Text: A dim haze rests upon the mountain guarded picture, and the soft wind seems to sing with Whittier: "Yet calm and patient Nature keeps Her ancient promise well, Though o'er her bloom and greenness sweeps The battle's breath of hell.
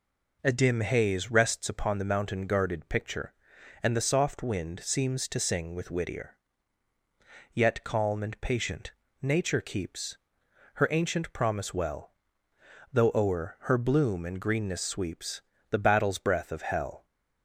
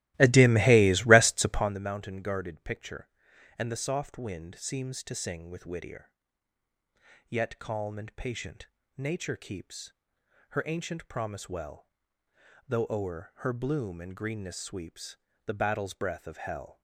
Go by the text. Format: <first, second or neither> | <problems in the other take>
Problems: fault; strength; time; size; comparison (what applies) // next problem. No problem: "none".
first | starts louder than the rest; strong; until 1.8 s; 16.5 dB // pauses between "patient" and "Nature"; slight; at 8.6 s; 0.28 s long; slight in the first // pauses between "keeps" and "Her"; noticeable; at 9.9 s; 0.58 s long; noticeable in the first // pauses between "sweeps" and "The"; slight; at 15.1 s; 0.30 s long; slight in the first